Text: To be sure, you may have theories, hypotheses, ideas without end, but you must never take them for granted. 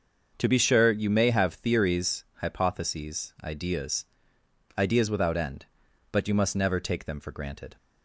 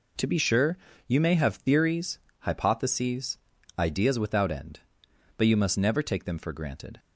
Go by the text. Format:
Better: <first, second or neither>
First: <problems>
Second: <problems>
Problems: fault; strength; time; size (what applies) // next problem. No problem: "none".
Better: second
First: starts louder than the rest; until 1.3 s; 6.5 dB // says "ideas" twice; at 4.7 s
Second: none